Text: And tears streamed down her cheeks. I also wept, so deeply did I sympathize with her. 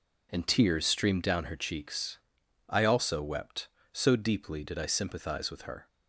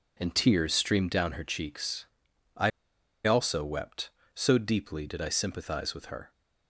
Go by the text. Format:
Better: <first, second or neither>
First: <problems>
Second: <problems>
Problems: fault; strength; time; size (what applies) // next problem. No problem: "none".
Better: first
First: none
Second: pauses between "I" and "also"; noticeable; at 2.7 s; 0.54 s long